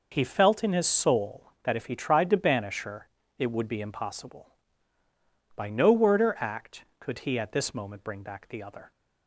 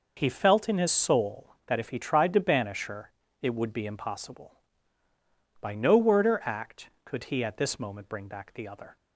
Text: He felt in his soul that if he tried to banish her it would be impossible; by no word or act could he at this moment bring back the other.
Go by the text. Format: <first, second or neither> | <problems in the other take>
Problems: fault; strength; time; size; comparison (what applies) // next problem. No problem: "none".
neither | pauses between "her" and "it"; slight; the same in both